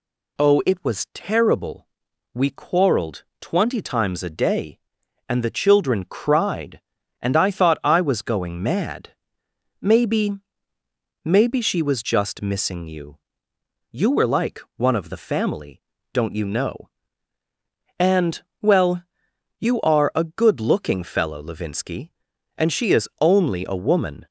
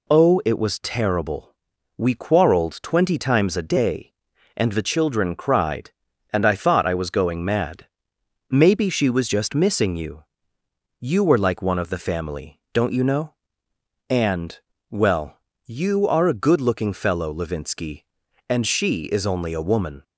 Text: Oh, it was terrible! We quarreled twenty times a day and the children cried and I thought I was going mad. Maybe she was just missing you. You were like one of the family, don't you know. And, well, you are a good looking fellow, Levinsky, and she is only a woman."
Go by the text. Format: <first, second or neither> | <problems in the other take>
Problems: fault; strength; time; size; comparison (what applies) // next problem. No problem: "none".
second | pauses between "quarreled" and "twenty"; slight; at 3.2 s; 0.18 s long // says "Maybe" twice; at 11.2 s // pauses between "like" and "one"; slight; at 14.6 s; 0.16 s long